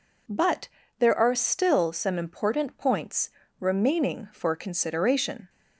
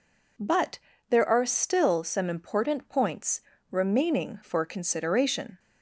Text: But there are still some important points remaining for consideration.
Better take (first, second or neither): neither